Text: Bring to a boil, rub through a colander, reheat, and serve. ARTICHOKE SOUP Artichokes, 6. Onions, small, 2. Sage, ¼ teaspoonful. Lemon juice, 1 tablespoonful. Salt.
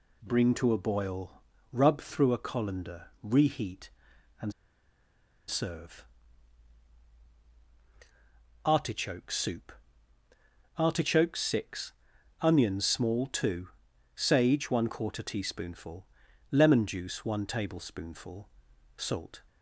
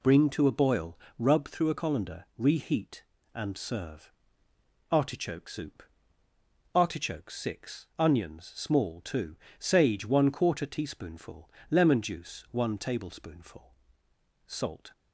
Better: second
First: pauses between "and" and "serve"; noticeable; at 4.5 s; 0.95 s long // pauses between "SOUP" and "Artichokes"; at 9.7 s; 1.0 s long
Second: pauses between "SOUP" and "Artichokes"; noticeable; at 5.8 s; 0.90 s long

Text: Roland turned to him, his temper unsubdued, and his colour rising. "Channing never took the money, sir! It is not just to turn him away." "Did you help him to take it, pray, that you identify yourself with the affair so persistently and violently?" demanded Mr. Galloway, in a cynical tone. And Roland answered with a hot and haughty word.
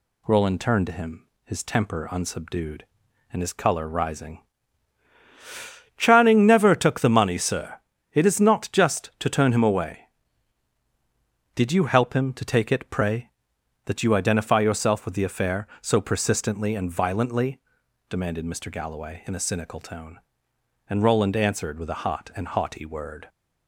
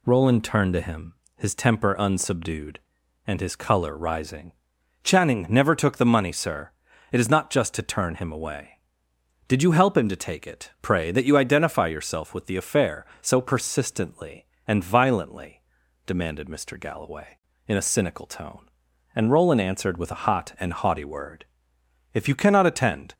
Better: first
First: none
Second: goes on to say "If you cannot attend"; noticeable; from 22.1 s on; 1.0 s long

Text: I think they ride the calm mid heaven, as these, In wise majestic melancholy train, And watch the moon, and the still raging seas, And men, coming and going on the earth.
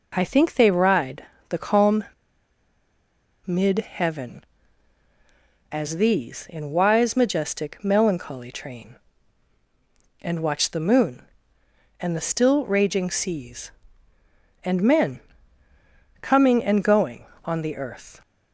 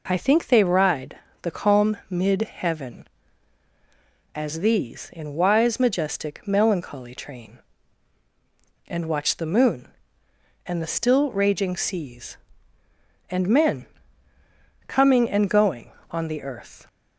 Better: second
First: pauses between "ride" and "the"; slight; at 1.2 s; 0.24 s long // pauses between "calm" and "mid"; strong; at 2.0 s; 1.4 s long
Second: pauses between "ride" and "the"; slight; at 1.1 s; 0.24 s long

